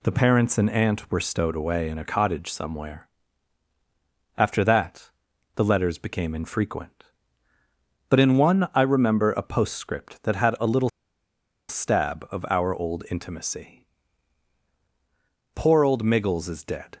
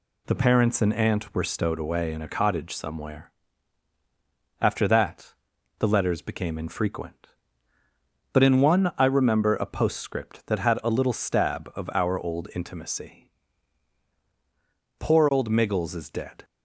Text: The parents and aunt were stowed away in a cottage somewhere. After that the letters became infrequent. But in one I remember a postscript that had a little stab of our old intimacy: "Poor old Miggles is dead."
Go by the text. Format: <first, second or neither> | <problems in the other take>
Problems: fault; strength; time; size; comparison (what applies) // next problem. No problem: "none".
second | pauses between "that" and "the"; noticeable; at 5.0 s; 0.46 s long; noticeable in the second // pauses between "little" and "stab"; noticeable; at 10.8 s; 0.80 s long